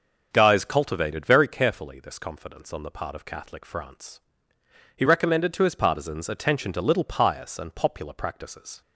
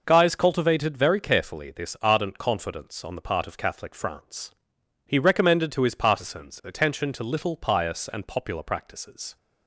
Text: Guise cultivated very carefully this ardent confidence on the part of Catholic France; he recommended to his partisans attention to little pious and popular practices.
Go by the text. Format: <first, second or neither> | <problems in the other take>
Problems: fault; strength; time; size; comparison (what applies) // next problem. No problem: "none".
second | skips "ardent"; at 2.1 s